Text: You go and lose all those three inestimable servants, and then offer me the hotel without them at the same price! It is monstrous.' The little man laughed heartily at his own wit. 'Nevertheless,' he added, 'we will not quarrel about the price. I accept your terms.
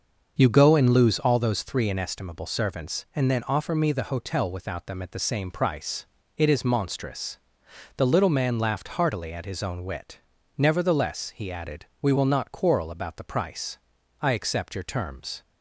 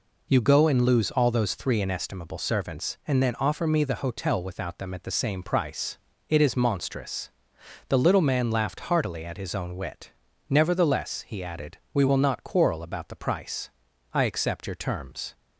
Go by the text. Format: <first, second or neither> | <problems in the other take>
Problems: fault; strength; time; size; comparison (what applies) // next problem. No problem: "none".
second | starts louder than the rest; until 1.4 s; 6.5 dB